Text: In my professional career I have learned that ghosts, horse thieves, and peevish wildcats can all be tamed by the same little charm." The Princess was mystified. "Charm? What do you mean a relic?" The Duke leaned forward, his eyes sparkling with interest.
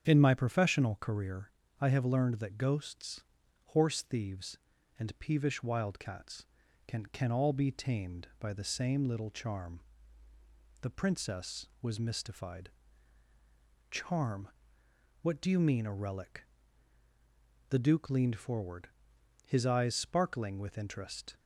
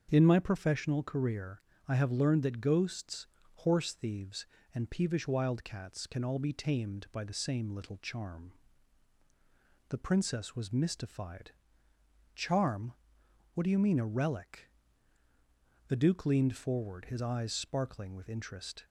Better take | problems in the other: second | starts louder than the rest; strong; until 1.1 s; 9 dB; also in the second // pauses between "career" and "I"; slight; at 1.4 s; 0.32 s long; slight in the second // says "can" twice; at 7.0 s

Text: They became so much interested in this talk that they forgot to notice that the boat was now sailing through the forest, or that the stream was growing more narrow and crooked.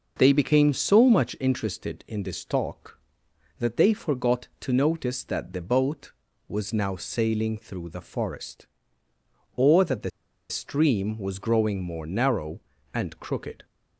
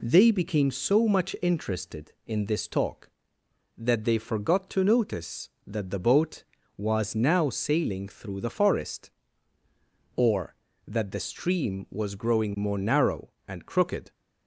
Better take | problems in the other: second | pauses between "the" and "stream"; at 10.0 s; 0.40 s long

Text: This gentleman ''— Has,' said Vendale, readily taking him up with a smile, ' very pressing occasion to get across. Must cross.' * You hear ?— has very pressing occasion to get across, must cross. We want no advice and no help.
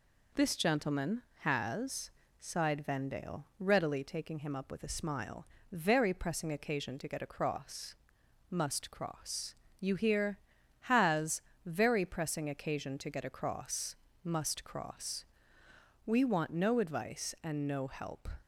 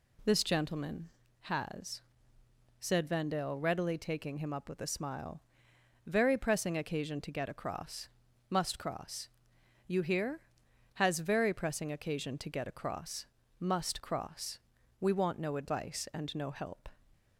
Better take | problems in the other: second | says "sighed" for "said"; at 2.4 s // pauses between "has" and "very"; slight; at 11.4 s; 0.24 s long

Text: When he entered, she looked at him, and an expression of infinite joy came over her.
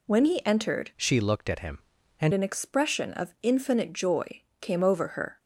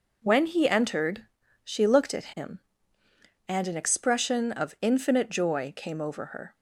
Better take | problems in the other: second | changes voice from "she" to "and"; from 0.9 to 2.3 s; 1.4 s long // pauses between "joy" and "came"; slight; at 4.4 s; 0.20 s long

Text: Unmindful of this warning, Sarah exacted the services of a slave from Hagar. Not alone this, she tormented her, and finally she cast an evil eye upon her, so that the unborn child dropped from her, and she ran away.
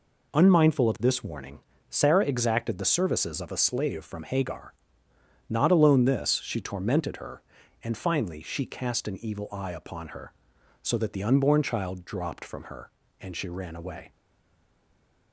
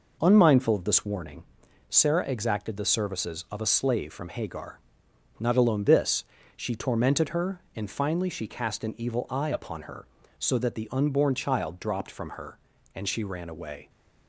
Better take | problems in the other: second | stays silent after the last word; noticeable; from 14.1 s on; 1.2 s long

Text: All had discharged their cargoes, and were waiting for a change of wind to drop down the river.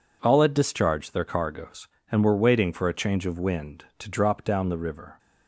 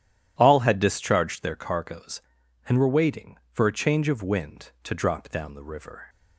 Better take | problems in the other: neither | none

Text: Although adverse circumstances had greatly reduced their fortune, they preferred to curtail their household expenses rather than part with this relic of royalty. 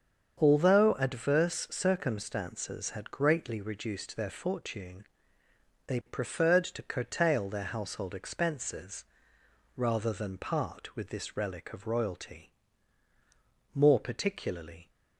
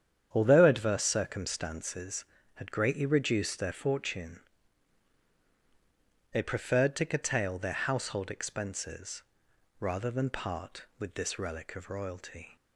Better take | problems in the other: second | starts louder than the rest; strong; until 1.4 s; 7.5 dB; strong in the second // pauses between "expenses" and "rather"; noticeable; at 9.0 s; 0.72 s long; noticeable in the second // goes on to say "More particularly"; noticeable; from 13.7 s on; 1.1 s long

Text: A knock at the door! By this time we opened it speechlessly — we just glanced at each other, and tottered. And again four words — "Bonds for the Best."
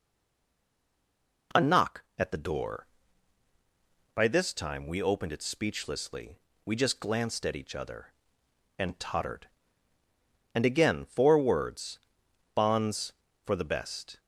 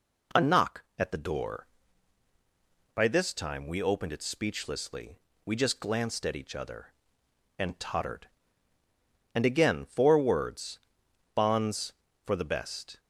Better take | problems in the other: second | stays silent before the first word; noticeable; until 1.5 s; 1.5 s long

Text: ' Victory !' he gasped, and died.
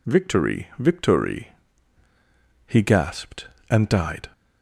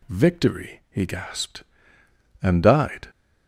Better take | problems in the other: second | says "Victory" twice; at 0.7 s

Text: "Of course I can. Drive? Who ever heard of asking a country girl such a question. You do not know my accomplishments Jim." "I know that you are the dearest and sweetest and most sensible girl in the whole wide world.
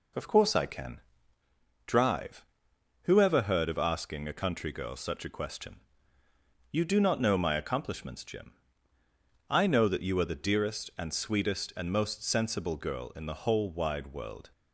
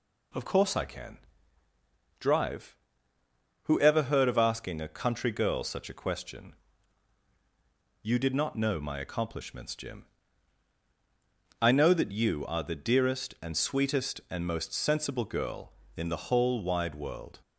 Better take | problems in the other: first | says "did" for "do"; at 8.1 s

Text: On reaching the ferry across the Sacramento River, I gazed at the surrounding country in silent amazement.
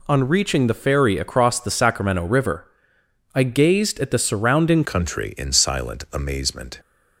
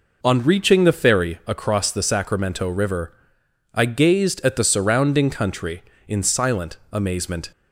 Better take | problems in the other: second | changes voice at "country"; from 4.8 s on; 1.9 s long

